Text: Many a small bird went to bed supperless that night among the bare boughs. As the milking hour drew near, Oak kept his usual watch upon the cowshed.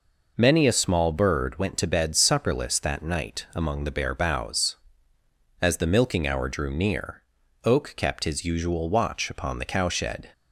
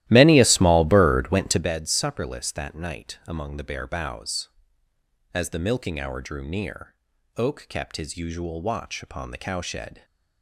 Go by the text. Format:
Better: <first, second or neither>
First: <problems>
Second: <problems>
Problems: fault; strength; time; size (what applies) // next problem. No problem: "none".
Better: first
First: none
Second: starts louder than the rest; strong; until 1.7 s; 15 dB